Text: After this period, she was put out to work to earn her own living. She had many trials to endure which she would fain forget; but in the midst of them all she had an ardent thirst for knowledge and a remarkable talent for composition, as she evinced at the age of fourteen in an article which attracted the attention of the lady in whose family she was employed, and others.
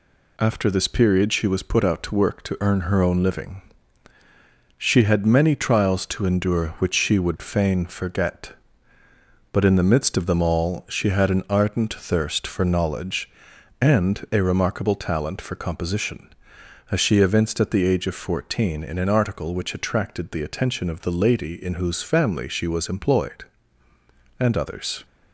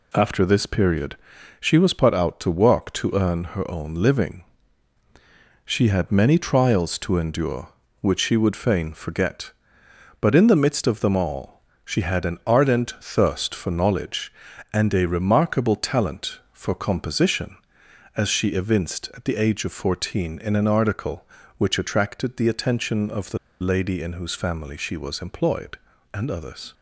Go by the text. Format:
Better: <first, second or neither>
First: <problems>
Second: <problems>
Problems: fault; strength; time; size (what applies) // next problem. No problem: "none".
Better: first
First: none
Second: pauses between "all" and "she"; slight; at 11.6 s; 0.20 s long // pauses between "the" and "lady"; slight; at 23.3 s; 0.23 s long